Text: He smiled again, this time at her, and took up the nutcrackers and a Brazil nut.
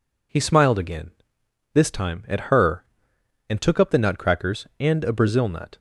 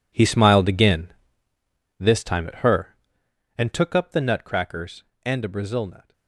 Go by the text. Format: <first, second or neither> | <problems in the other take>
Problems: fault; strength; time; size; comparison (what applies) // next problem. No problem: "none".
first | gets quieter; strong; throughout; 16.5 dB